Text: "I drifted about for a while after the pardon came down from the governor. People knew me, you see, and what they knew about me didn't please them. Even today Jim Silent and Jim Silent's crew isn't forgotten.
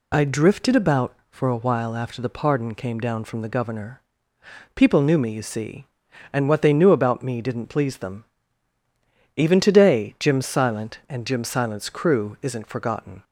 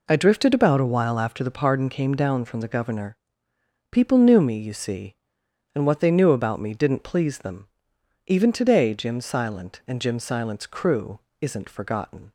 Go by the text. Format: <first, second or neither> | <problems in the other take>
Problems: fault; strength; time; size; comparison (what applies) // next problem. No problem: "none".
first | skips "for"; at 0.7 s // pauses between "crew" and "isn't"; slight; at 11.1 s; 0.22 s long